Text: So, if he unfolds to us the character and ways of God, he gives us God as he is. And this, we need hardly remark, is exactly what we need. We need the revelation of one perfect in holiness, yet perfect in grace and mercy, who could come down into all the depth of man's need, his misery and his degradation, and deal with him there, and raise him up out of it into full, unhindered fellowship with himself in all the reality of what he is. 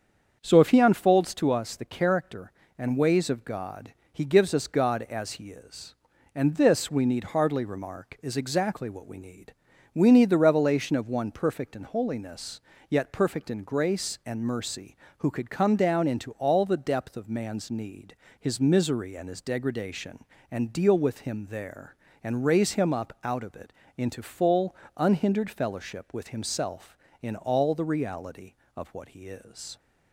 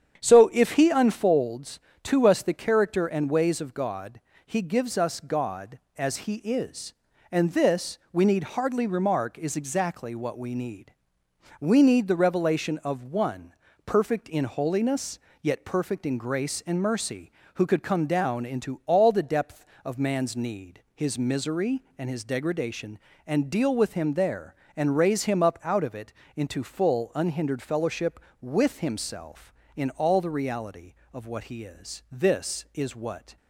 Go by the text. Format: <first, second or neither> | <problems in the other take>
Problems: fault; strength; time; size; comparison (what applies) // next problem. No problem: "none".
first | starts louder than the rest; strong; until 1.2 s; 8.5 dB; strong in the first // pauses between "one" and "perfect"; slight; at 13.5 s; 0.34 s long // pauses between "it" and "into"; slight; at 26.1 s; 0.22 s long; slight in the first // goes on to say "This is what"; noticeable; from 32.1 s on; 1.2 s long